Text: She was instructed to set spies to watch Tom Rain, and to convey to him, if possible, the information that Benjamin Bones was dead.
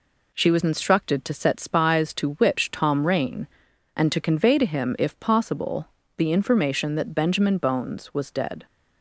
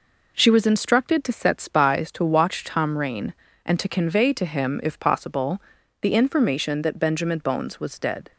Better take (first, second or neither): second